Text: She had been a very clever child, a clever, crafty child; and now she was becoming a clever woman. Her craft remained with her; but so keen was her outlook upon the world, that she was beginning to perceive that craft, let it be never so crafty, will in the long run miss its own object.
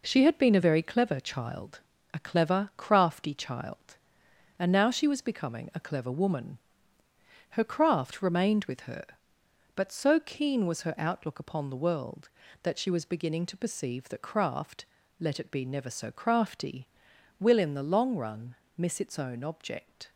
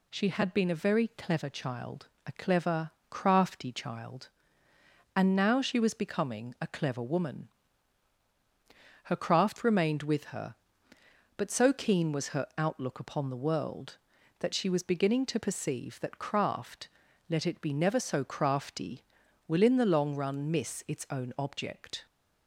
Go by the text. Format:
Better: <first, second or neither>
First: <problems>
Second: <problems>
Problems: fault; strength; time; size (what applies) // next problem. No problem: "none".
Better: second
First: gets quieter; throughout; 6.5 dB // pauses between "run" and "miss"; slight; at 18.5 s; 0.20 s long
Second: none